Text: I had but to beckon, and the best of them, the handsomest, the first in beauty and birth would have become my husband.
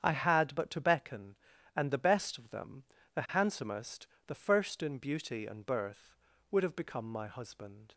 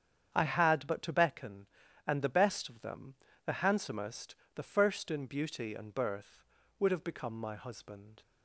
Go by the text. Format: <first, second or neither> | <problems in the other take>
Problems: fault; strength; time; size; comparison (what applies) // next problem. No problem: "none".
neither | starts louder than the rest; strong; the same in both